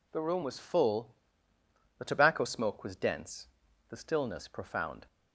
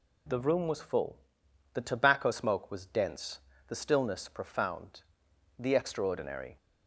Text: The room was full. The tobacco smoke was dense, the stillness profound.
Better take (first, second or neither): first